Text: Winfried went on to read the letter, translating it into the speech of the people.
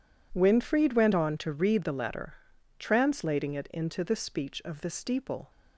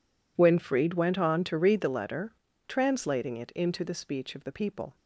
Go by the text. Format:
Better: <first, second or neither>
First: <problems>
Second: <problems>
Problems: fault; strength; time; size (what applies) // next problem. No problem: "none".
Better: second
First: says "steeple" for "people"; at 4.8 s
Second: none